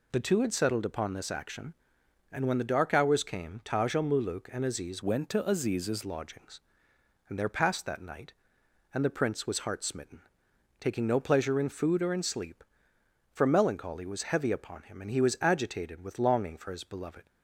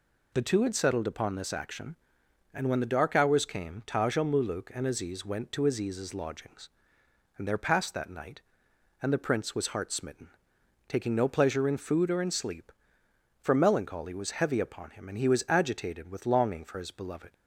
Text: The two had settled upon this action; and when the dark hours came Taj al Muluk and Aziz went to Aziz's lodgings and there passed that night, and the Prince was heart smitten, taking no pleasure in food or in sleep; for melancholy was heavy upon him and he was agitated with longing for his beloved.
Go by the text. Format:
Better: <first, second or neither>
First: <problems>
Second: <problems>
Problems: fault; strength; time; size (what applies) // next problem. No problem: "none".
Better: second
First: changes voice from "went" to "Aziz's"; from 5.0 to 6.0 s; 1.0 s long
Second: none